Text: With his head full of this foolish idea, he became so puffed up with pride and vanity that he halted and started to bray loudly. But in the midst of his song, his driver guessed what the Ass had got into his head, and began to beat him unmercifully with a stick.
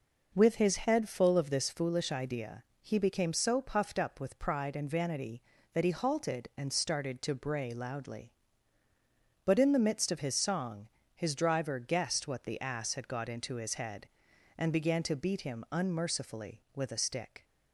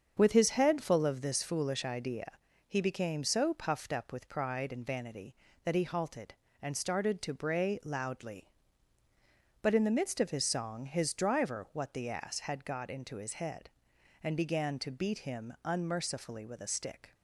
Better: first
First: none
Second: starts louder than the rest; strong; until 1.1 s; 7 dB // skips "guessed"; at 11.6 s

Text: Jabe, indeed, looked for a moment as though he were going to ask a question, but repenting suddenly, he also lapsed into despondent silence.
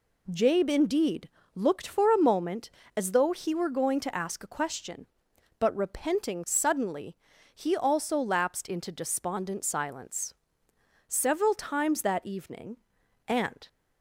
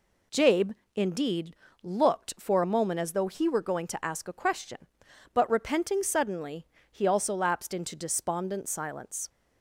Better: second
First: goes on to say "Several times that evening and"; strong; from 11.0 s on; 2.6 s long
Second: none

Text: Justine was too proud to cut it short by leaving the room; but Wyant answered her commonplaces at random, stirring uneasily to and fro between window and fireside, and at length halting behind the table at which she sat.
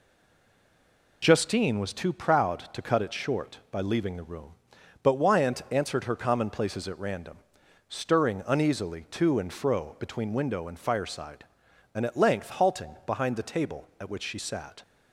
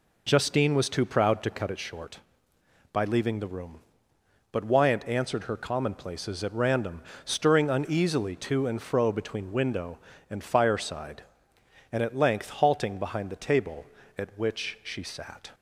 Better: second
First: stays silent before the first word; noticeable; until 1.2 s; 1.2 s long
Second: none

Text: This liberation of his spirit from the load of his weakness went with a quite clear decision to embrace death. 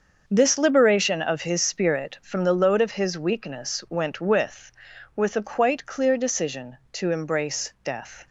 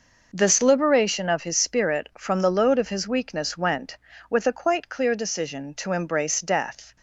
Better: second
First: starts louder than the rest; until 1.2 s; 6.5 dB // says "with" twice; at 5.1 s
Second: none

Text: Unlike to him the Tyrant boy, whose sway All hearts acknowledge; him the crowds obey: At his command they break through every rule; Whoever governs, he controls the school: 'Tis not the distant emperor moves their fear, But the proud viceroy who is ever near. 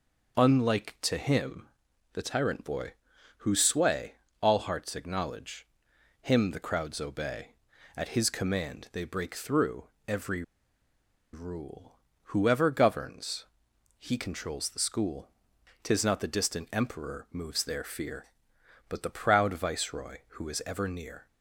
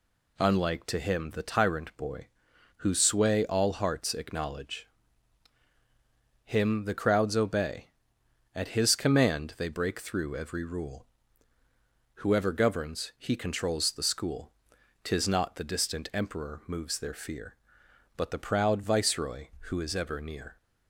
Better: second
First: pauses between "him" and "the"; noticeable; at 1.6 s; 0.48 s long // pauses between "sway" and "All"; slight; at 4.1 s; 0.26 s long // pauses between "through" and "every"; slight; at 9.8 s; 0.20 s long // pauses between "every" and "rule"; noticeable; at 10.4 s; 0.90 s long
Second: none

